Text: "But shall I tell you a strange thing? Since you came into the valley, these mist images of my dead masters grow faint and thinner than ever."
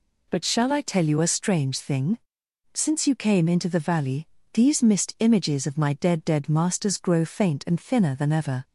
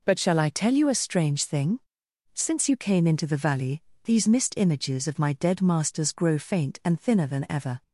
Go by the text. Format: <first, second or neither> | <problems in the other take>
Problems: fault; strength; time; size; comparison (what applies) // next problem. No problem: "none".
second | says "dead" twice; at 6.2 s